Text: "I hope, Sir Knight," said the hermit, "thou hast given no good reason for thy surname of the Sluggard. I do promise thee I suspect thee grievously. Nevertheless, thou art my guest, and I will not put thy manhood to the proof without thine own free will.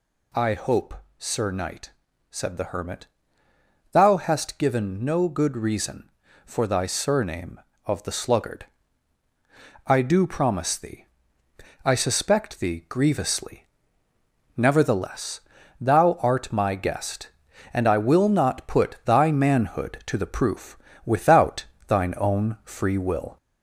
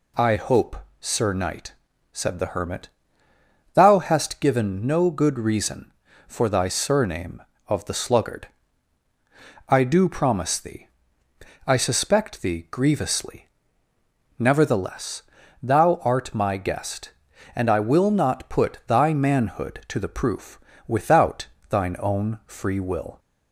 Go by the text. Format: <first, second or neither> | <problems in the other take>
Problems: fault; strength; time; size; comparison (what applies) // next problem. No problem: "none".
second | gets louder; slight; throughout; 2.5 dB // pauses between "thee" and "I"; noticeable; at 11.0 s; 0.80 s long; noticeable in the second // pauses between "proof" and "without"; slight; at 20.7 s; 0.26 s long; slight in the second // pauses between "without" and "thine"; slight; at 21.6 s; 0.24 s long; slight in the second